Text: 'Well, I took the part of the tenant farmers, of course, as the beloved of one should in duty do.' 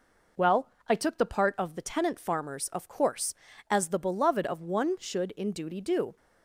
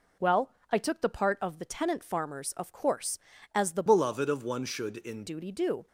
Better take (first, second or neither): first